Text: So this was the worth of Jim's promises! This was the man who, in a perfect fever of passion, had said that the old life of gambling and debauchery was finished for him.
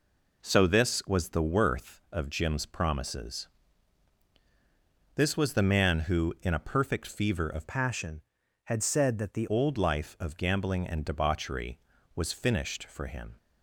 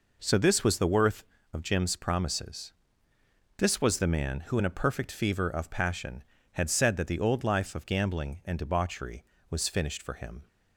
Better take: second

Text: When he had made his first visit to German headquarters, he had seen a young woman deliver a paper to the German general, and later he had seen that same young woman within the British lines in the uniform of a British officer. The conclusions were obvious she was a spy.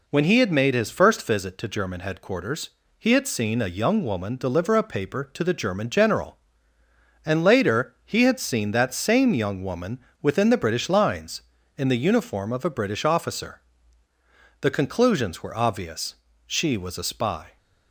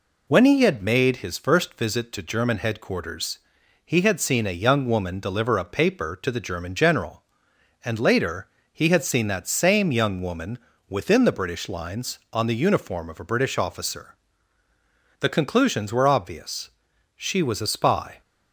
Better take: first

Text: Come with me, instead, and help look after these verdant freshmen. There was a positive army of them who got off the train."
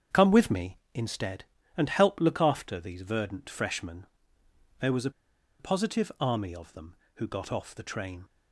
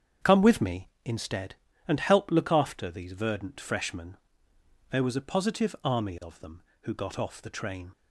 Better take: second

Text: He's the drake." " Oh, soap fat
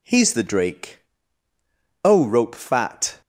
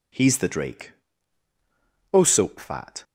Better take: second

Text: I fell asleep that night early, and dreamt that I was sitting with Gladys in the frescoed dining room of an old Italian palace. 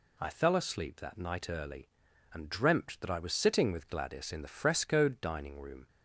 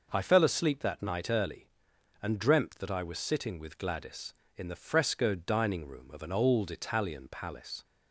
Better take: second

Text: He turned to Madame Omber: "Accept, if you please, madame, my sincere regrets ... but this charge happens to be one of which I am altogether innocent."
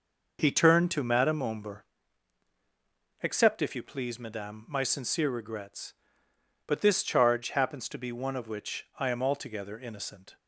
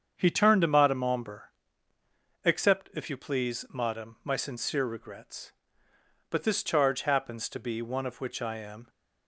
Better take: first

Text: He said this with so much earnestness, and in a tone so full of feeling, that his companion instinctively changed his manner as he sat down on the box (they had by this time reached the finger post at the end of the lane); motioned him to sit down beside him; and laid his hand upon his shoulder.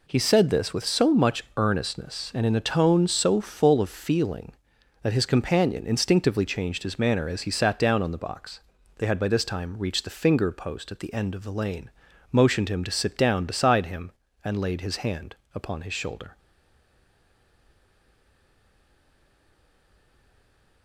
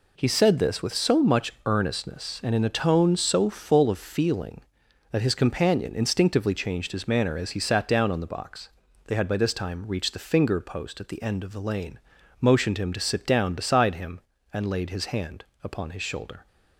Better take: second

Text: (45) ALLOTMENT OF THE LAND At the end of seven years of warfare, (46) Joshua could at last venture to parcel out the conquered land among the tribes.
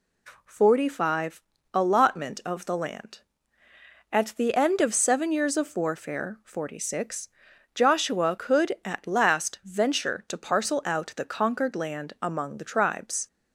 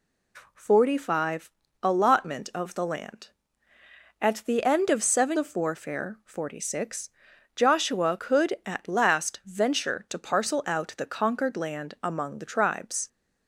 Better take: first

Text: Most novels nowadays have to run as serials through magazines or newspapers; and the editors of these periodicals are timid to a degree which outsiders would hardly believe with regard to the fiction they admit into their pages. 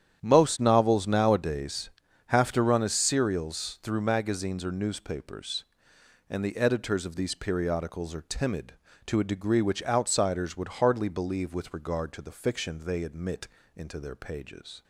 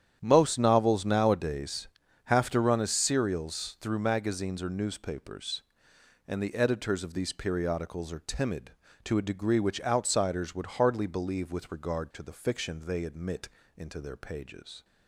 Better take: neither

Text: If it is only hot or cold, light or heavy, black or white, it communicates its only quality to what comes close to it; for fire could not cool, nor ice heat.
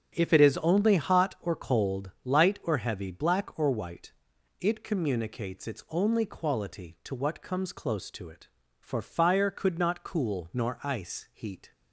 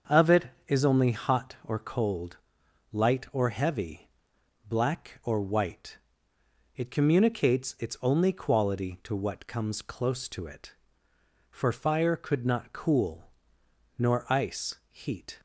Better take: first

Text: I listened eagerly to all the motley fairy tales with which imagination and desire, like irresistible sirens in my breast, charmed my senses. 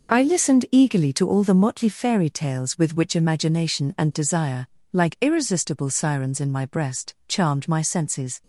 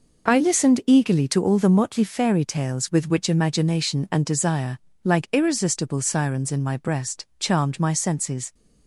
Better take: neither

